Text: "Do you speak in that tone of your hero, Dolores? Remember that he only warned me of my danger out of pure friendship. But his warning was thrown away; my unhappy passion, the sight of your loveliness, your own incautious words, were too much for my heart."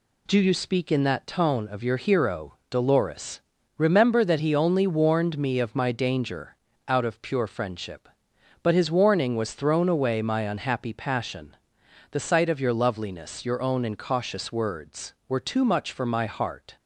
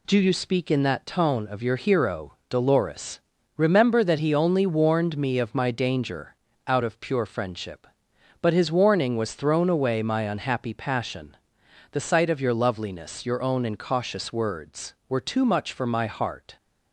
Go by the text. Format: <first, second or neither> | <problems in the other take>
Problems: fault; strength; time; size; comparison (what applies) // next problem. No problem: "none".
neither | pauses between "danger" and "out"; slight; the same in both